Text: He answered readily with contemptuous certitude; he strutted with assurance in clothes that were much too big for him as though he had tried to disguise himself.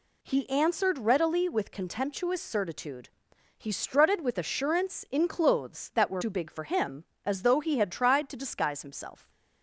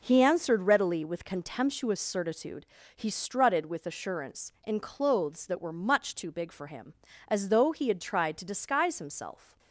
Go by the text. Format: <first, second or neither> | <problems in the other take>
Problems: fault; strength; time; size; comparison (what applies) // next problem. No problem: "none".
second | skips "much"; at 6.2 s